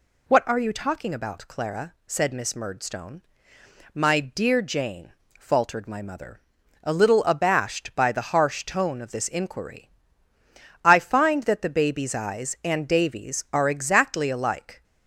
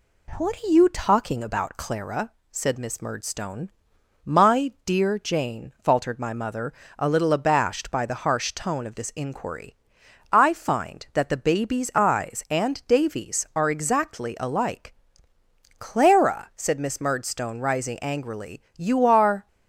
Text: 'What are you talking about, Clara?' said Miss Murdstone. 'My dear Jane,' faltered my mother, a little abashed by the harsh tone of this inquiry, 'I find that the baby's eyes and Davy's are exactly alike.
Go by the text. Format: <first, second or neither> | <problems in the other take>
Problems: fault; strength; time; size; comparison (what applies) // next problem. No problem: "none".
first | goes on to say "Clara said Miss Murdstone rising angrily you are"; strong; from 15.7 s on; 3.6 s long